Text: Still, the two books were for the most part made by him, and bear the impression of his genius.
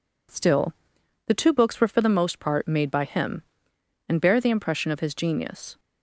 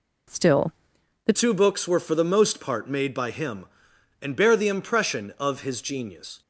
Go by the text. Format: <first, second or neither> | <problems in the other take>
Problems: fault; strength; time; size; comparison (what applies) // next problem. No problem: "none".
first | changes voice at "two"; from 1.3 s on; 5.1 s long